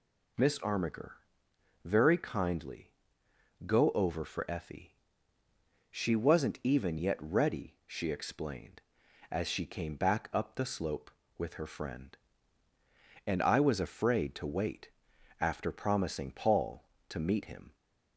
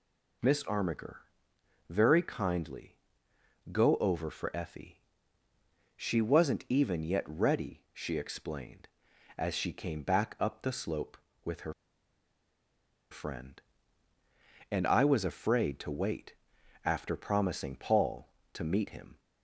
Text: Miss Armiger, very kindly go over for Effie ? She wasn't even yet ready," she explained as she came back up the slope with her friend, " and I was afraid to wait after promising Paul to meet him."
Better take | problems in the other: first | pauses between "kindly" and "go"; noticeable; at 2.9 s; 0.78 s long; noticeable in the first // pauses between "her" and "friend"; strong; at 11.7 s; 1.3 s long // pauses between "wait" and "after"; noticeable; at 16.3 s; 0.50 s long; noticeable in the first

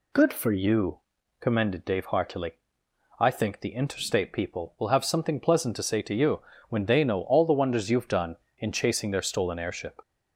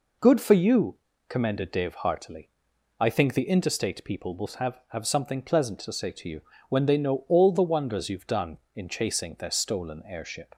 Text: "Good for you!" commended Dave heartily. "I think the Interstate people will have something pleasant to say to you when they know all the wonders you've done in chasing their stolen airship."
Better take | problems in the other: first | says "have" twice; at 4.9 s // pauses between "you" and "when"; slight; at 6.4 s; 0.28 s long; slight in the first

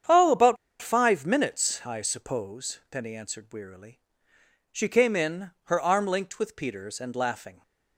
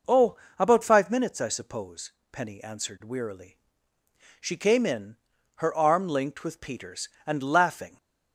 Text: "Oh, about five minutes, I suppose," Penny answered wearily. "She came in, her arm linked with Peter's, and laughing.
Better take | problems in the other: second | starts louder than the rest; strong; until 1.3 s; 8 dB // pauses between "about" and "five"; slight; at 0.5 s; 0.25 s long

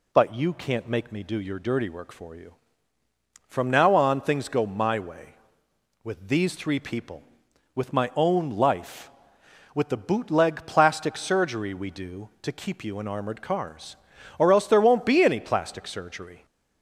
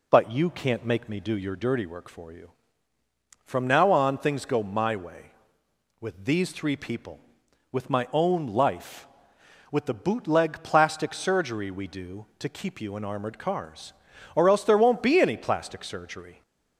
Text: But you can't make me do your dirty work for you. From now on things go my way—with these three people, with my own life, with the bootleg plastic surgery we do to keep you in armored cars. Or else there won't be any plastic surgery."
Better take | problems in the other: first | starts louder than the rest; slight; until 1.9 s; 2.5 dB

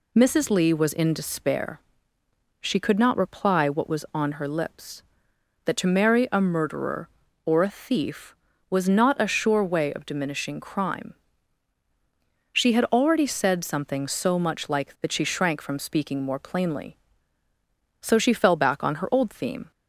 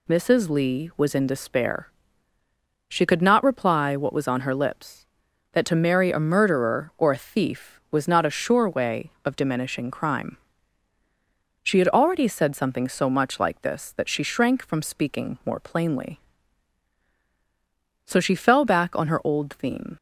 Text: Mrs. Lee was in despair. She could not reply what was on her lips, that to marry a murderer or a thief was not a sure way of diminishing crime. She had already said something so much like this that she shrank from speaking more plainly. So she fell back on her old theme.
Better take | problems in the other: second | skips "this"; at 14.9 s

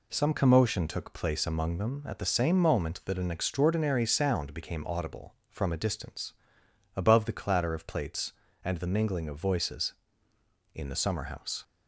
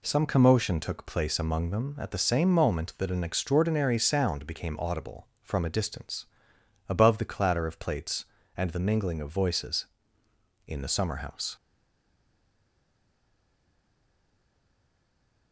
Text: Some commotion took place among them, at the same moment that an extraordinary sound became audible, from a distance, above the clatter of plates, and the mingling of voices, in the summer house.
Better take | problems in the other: first | stays silent after the last word; strong; from 11.5 s on; 4.0 s long

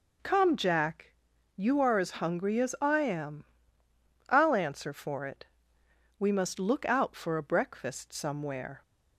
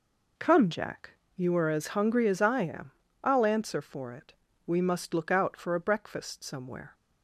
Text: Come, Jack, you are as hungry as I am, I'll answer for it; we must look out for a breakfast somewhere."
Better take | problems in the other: neither | none

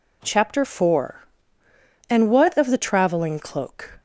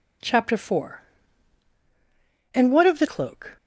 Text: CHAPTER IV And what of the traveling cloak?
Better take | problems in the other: first | skips "traveling"; at 3.0 s

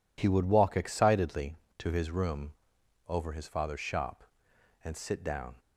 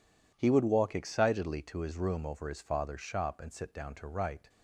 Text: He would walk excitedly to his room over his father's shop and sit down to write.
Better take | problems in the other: second | pauses between "room" and "over"; noticeable; at 2.5 s; 0.56 s long // stops before "to write"; at 5.5 s

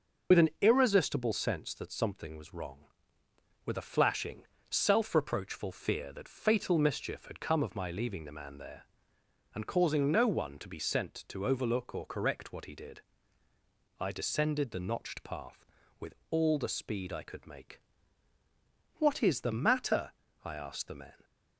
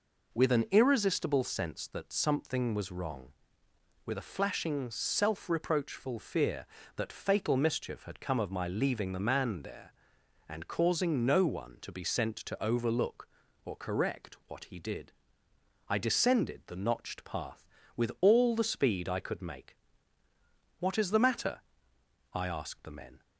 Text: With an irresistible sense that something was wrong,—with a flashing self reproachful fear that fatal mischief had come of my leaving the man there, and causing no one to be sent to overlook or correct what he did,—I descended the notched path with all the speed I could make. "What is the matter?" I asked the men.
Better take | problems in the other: second | loses the start of "With"; at 0.3 s; 45 ms // pauses between "flashing" and "self"; slight; at 4.4 s; 0.22 s long // pauses between "with" and "all"; slight; at 16.1 s; 0.16 s long

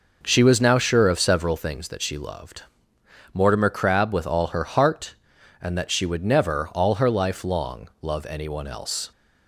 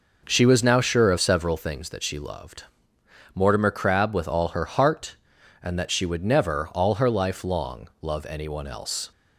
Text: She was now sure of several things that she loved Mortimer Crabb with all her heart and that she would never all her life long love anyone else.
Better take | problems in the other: neither | pauses between "loved" and "Mortimer"; noticeable; the same in both

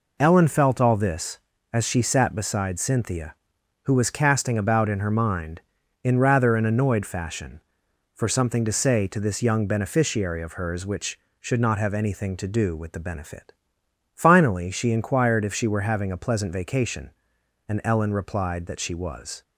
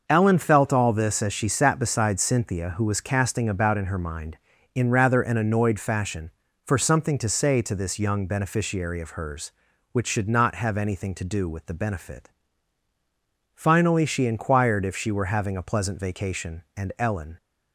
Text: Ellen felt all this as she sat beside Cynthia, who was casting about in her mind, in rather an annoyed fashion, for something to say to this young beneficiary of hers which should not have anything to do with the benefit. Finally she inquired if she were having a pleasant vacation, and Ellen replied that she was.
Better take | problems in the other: first | starts louder than the rest; noticeable; until 1.0 s; 6 dB // stops before "replied that she was"; at 17.3 s

